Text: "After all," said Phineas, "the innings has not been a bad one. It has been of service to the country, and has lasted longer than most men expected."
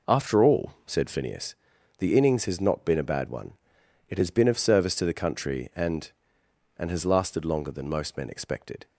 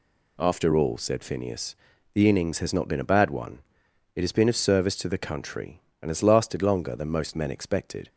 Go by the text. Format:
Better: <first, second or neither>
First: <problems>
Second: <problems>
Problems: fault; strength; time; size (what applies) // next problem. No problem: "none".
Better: second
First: says "and" twice; at 6.7 s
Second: none